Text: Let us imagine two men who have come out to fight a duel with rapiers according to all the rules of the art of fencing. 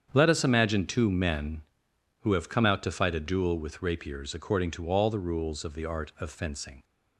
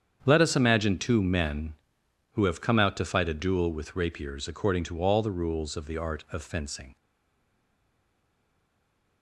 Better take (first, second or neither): first